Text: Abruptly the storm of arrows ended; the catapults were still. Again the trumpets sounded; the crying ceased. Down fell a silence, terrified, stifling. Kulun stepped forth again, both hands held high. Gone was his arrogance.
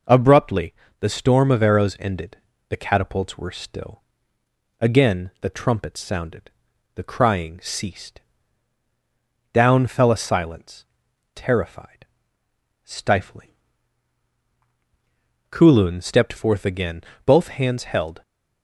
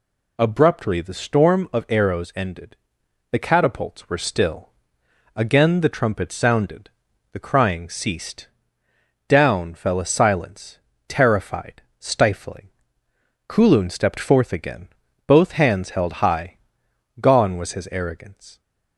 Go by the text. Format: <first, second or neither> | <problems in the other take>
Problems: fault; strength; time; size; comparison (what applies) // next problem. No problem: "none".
second | pauses between "Abruptly" and "the"; slight; at 0.7 s; 0.26 s long // stops before "high Gone was his arrogance"; at 18.2 s